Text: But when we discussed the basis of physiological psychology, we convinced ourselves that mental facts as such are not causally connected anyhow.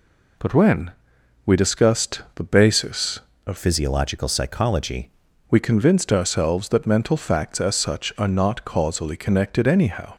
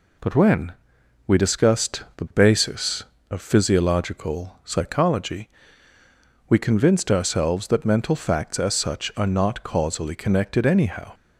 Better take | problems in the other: second | pauses between "when" and "we"; noticeable; at 0.9 s; 0.54 s long; noticeable in the second // changes voice from "physiological" to "psychology"; from 3.5 to 5.1 s; 1.6 s long

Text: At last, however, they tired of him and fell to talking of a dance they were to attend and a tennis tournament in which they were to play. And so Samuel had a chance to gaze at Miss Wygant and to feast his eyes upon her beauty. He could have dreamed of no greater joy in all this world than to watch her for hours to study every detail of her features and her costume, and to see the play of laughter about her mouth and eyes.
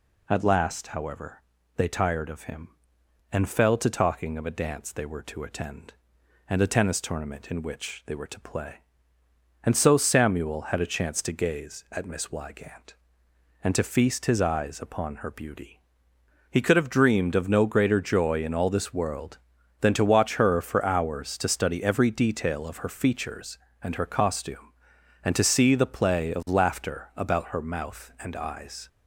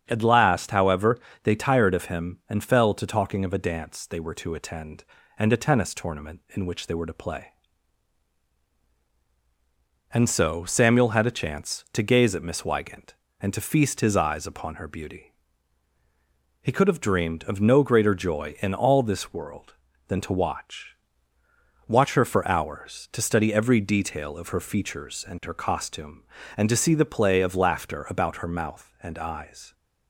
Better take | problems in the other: first | starts louder than the rest; strong; until 1.0 s; 7.5 dB // says "watch" twice; at 21.8 s

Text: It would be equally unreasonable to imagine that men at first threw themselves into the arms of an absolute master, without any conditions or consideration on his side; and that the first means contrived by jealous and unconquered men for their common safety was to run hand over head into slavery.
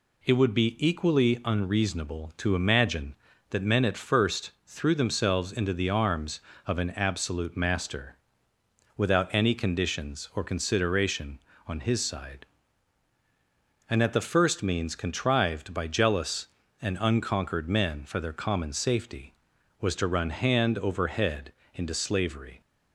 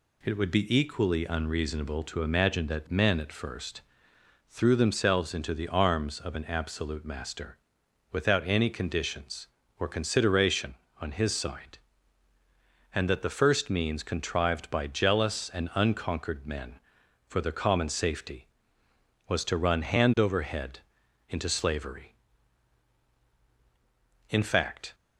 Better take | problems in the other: first | pauses between "first" and "threw"; noticeable; at 3.8 s; 0.66 s long // pauses between "head" and "into"; noticeable; at 20.7 s; 0.50 s long; slight in the first // goes on to say "In fact"; noticeable; from 24.3 s on; 0.64 s long

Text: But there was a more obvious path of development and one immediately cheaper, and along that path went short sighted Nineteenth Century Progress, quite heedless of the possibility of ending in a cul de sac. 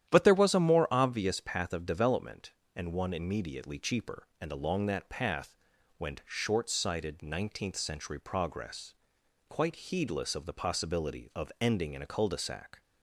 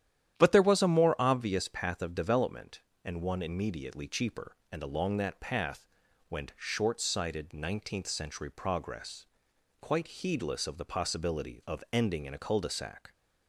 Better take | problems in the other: neither | starts louder than the rest; strong; the same in both // pauses between "path" and "went"; the same in both

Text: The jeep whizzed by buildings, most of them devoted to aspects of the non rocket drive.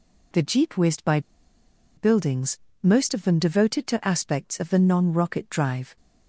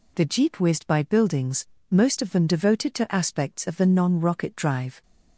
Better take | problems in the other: second | pauses between "by" and "buildings"; noticeable; at 1.1 s; 0.77 s long

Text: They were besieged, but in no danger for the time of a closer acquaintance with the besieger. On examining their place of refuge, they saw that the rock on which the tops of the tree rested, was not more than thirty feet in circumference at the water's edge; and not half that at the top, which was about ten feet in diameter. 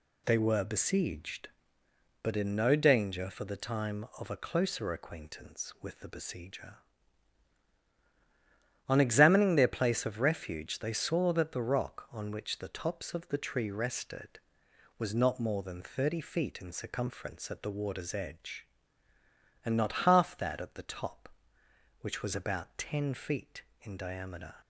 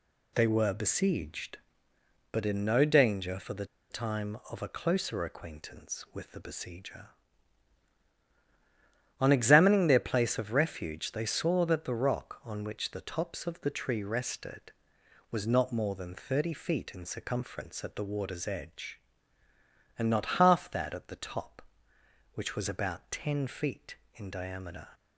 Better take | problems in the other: first | pauses between "the" and "time"; slight; at 3.6 s; 0.24 s long

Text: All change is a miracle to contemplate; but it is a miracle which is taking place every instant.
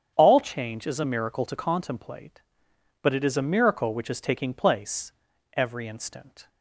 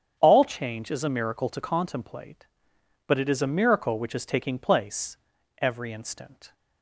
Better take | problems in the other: neither | starts louder than the rest; strong; the same in both // pauses between "place" and "every"; the same in both

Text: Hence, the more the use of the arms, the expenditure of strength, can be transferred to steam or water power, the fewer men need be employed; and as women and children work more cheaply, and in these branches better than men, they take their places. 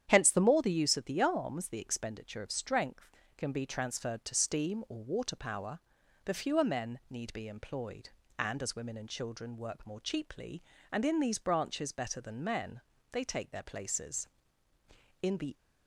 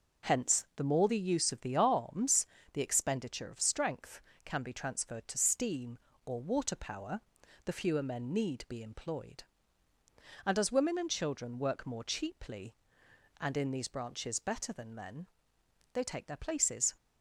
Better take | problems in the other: second | starts louder than the rest; strong; until 1.1 s; 9.5 dB // goes on to say "In the"; slight; from 15.2 s on; 0.32 s long

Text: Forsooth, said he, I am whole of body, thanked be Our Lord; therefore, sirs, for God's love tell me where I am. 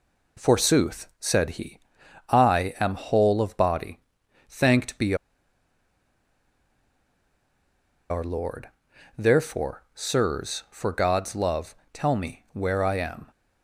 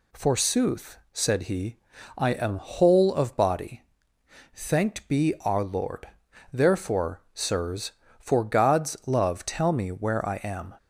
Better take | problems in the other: second | pauses between "be" and "Our"; strong; at 5.1 s; 2.9 s long // pauses between "love" and "tell"; slight; at 11.7 s; 0.18 s long

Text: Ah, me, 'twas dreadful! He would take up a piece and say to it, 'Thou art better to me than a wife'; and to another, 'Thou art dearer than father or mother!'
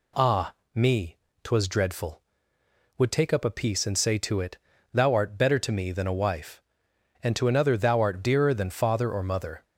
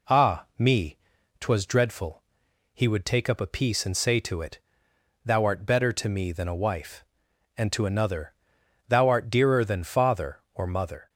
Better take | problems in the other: second | skips "He"; at 2.5 s

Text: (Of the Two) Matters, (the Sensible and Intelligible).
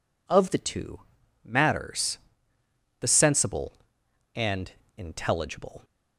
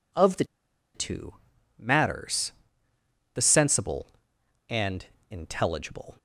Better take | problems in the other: first | pauses between "the" and "Two"; noticeable; at 0.4 s; 0.50 s long // pauses between "and" and "Intelligible"; slight; at 5.0 s; 0.24 s long; slight in the first

